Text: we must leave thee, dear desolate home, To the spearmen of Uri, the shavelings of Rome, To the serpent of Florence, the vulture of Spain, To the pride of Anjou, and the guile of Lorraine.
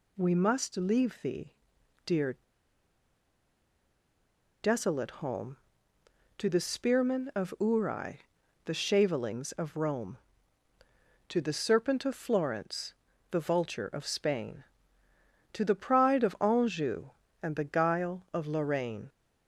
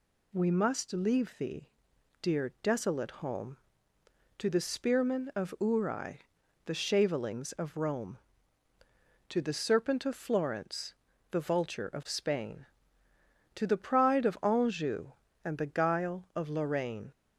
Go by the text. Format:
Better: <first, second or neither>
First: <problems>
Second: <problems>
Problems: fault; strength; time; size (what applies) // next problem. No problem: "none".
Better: second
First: pauses between "dear" and "desolate"; strong; at 2.3 s; 2.2 s long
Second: none